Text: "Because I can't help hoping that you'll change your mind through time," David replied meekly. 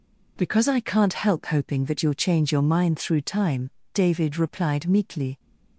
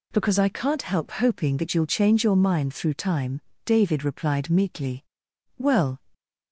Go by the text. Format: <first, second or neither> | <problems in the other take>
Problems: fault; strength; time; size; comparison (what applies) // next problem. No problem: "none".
first | goes on to say "Well"; slight; from 5.5 s on; 0.44 s long